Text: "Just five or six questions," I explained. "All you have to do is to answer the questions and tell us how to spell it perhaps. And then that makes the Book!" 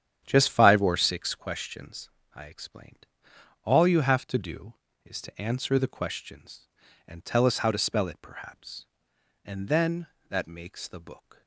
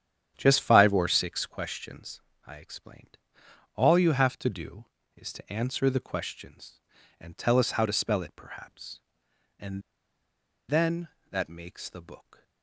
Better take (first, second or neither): first